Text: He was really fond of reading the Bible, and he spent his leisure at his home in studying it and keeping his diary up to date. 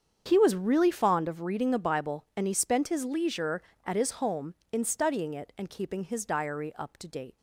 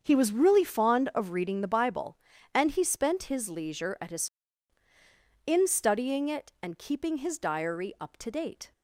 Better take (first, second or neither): first